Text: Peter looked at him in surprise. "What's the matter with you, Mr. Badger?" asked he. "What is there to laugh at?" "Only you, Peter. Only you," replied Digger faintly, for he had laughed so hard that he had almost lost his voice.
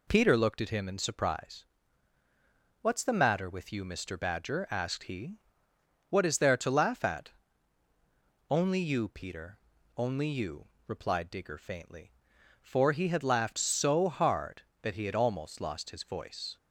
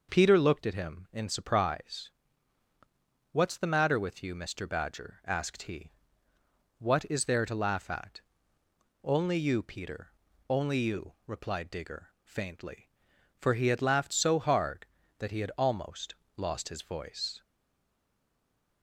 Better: first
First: none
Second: pauses between "almost" and "lost"; slight; at 16.1 s; 0.20 s long // stays silent after the last word; noticeable; from 17.4 s on; 1.4 s long

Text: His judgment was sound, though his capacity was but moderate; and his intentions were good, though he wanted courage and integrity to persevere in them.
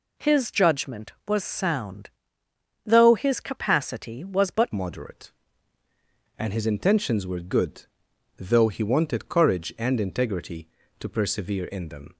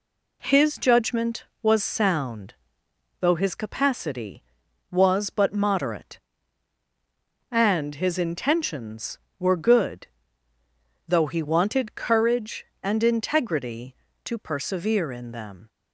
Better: second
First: changes voice at "moderate"; from 4.7 s on; 7.4 s long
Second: none

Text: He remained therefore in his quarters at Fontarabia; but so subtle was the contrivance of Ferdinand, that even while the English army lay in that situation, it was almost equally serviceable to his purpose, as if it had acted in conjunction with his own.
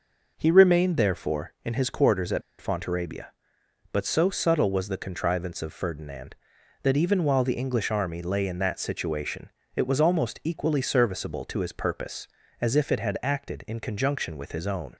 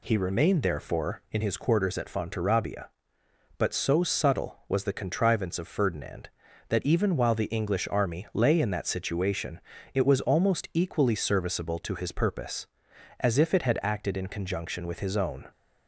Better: second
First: pauses between "at" and "Fontarabia"; slight; at 2.4 s; 0.19 s long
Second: none

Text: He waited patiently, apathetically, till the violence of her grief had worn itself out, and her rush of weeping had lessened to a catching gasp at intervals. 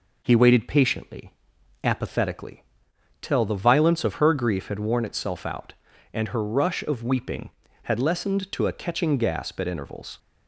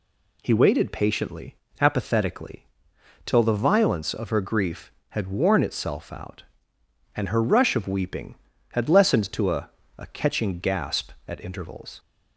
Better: first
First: none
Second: says "a" twice; at 9.9 s

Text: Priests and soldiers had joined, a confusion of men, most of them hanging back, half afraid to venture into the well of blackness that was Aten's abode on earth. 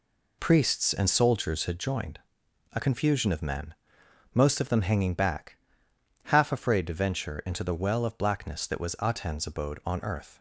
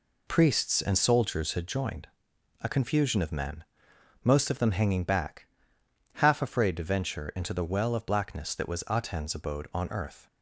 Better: neither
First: none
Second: none

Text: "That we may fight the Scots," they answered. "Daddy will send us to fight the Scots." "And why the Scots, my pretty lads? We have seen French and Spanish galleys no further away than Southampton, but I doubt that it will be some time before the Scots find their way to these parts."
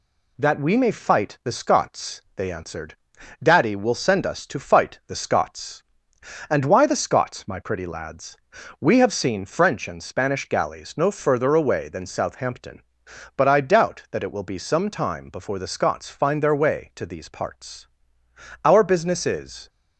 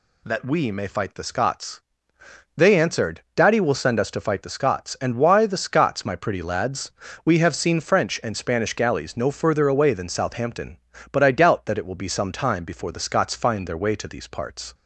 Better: second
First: goes on to say "Our business is"; noticeable; from 18.6 s on; 1.0 s long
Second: none

